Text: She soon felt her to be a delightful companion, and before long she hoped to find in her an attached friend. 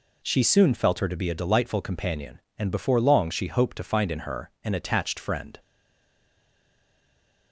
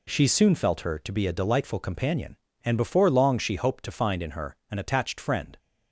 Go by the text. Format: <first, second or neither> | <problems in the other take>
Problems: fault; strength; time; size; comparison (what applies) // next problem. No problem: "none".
second | stays silent after the last word; noticeable; from 5.5 s on; 2.0 s long